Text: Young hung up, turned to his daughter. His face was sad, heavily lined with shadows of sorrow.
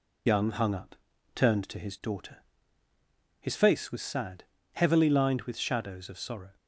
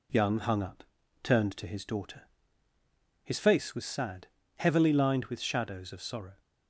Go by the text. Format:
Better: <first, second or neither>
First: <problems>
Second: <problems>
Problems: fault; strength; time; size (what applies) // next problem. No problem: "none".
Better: second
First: loses the start of "Young"; at 0.2 s; 40 ms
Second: none